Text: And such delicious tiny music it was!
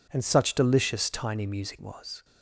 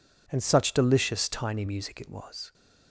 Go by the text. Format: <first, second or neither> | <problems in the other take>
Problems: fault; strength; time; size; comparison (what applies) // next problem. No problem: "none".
second | skips "it"; at 1.8 s